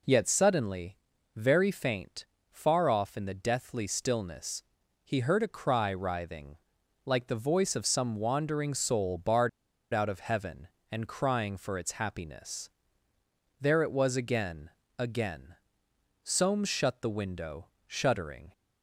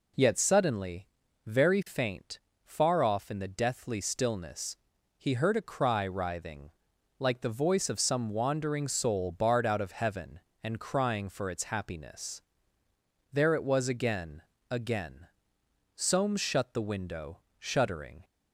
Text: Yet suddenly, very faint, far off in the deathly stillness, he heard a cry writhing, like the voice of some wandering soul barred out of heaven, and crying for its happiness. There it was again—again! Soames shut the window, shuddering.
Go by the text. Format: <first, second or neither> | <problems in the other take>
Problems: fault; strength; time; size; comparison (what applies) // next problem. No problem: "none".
second | pauses between "barred" and "out"; at 9.4 s; 0.44 s long